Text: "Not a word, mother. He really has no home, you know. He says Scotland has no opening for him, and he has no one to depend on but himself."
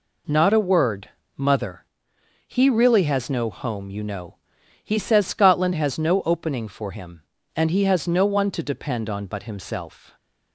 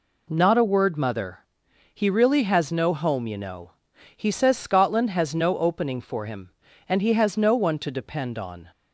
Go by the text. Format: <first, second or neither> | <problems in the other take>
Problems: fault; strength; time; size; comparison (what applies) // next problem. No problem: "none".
first | stops before "but himself"; at 8.7 s